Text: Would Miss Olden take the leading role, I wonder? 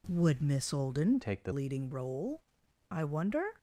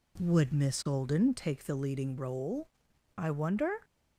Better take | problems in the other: second | changes voice from "take" to "the"; from 1.2 to 1.5 s; 0.3 s long

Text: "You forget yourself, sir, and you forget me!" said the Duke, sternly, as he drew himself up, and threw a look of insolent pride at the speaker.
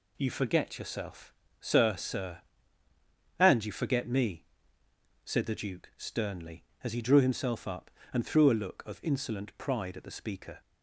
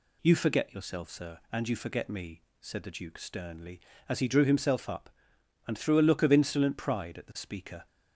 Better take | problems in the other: second | says "sir" twice; at 1.9 s

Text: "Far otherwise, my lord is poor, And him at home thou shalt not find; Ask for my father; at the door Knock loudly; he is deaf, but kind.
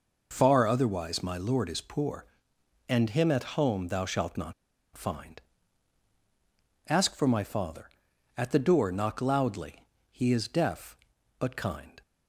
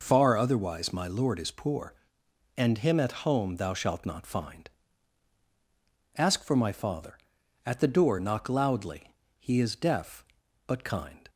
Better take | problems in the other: second | pauses between "not" and "find"; at 4.5 s; 0.42 s long

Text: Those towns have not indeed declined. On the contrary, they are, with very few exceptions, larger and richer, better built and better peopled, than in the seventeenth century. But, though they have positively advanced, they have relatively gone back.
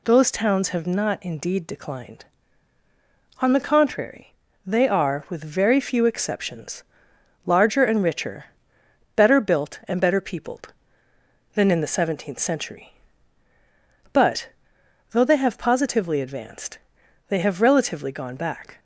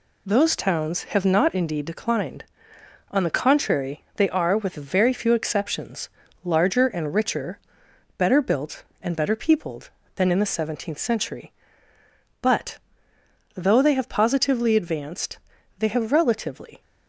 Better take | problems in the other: first | stops before "gone back"; at 16.8 s

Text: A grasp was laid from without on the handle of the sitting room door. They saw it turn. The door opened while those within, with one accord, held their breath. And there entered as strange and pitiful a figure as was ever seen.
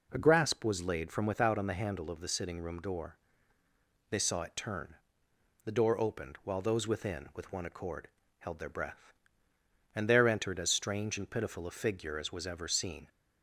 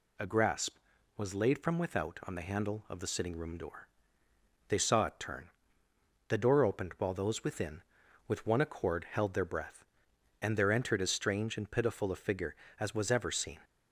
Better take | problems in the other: neither | none

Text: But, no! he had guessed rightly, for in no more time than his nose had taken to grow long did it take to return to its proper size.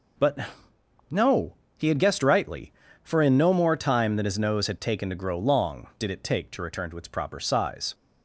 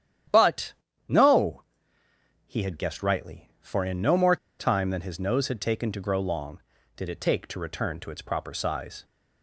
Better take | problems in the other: first | starts louder than the rest; strong; until 1.6 s; 10.5 dB // pauses between "more" and "time"; slight; at 4.3 s; 0.22 s long

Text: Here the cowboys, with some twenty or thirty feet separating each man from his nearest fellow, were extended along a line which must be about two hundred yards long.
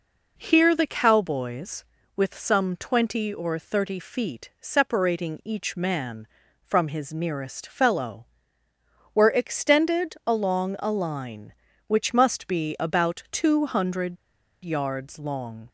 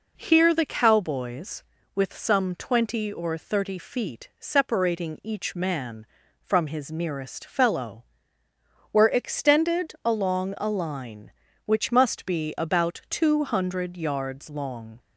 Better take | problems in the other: second | pauses between "hundred" and "yards"; noticeable; at 14.1 s; 0.48 s long

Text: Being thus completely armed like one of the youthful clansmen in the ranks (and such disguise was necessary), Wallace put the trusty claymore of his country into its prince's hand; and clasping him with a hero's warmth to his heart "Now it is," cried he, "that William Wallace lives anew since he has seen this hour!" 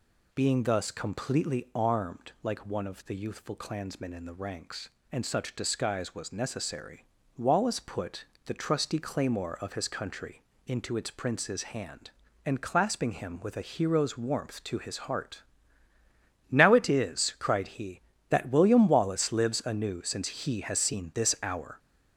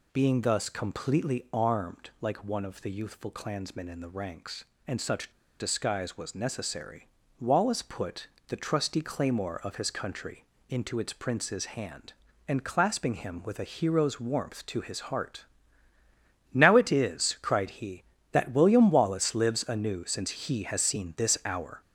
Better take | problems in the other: first | pauses between "such" and "disguise"; slight; at 5.2 s; 0.30 s long // pauses between "put" and "the"; slight; at 8.2 s; 0.22 s long; slight in the first // pauses between "country" and "into"; slight; at 10.4 s; 0.24 s long; slight in the first // pauses between "heart" and "Now"; at 15.4 s; 1.0 s long; also in the first

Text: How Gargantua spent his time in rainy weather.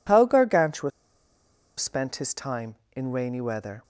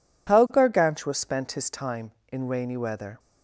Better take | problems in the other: second | pauses between "Gargantua" and "spent"; noticeable; at 0.8 s; 0.89 s long

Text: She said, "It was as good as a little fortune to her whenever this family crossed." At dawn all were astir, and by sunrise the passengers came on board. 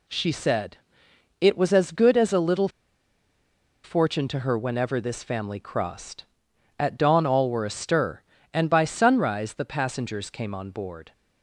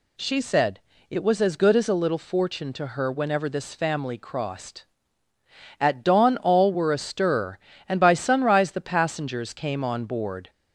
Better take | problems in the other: second | pauses between "little" and "fortune"; at 2.6 s; 1.1 s long

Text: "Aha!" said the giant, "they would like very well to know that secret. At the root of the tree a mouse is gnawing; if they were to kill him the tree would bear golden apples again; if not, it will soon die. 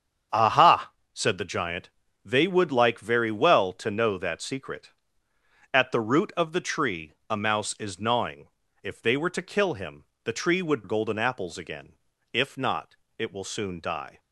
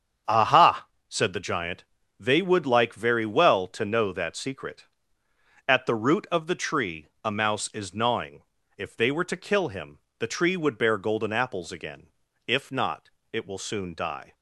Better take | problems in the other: second | starts louder than the rest; strong; until 1.5 s; 8 dB; strong in the second // pauses between "him" and "the"; slight; at 10.0 s; 0.18 s long; slight in the second // skips "bear"; at 10.8 s

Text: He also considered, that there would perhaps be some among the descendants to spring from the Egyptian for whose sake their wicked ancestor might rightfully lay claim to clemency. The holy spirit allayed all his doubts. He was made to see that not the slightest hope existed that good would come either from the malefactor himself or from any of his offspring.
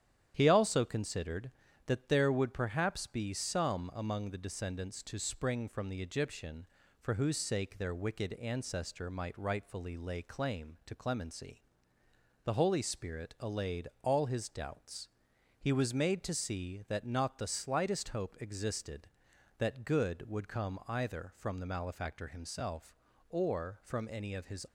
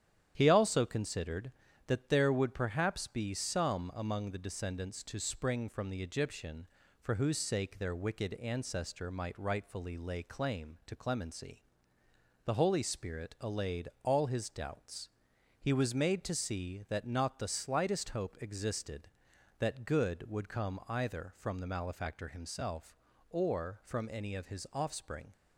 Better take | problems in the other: second | starts louder than the rest; strong; until 1.3 s; 10 dB; strong in the second // stops before "offspring"; at 24.6 s

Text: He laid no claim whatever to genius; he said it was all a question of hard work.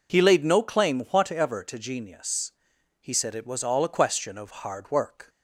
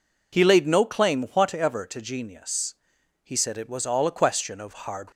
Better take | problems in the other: first | stops before "work"; at 5.1 s

